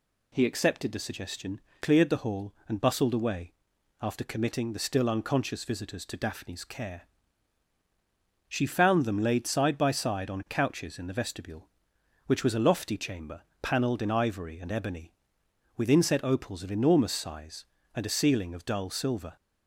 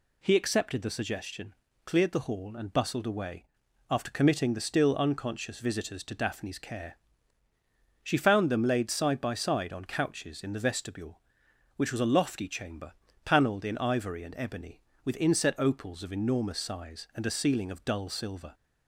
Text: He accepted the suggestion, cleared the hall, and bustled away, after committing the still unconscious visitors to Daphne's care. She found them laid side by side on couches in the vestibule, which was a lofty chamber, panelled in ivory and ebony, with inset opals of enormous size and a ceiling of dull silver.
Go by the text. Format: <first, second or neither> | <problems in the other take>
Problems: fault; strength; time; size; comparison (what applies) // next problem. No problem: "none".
neither | none